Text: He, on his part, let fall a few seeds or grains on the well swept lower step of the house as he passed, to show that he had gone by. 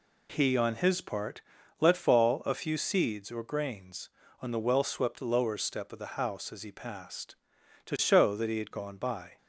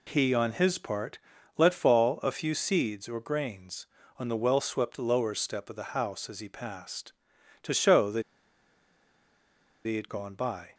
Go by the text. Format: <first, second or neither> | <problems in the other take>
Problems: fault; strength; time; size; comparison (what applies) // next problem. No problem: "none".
first | pauses between "that" and "he"; strong; at 8.2 s; 1.6 s long